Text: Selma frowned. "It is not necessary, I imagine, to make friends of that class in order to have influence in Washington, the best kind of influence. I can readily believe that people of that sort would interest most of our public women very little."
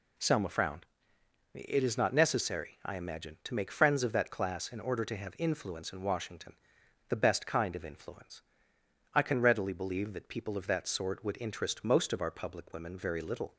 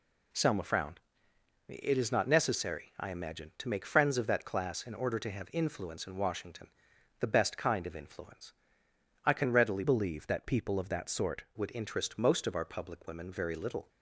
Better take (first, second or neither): first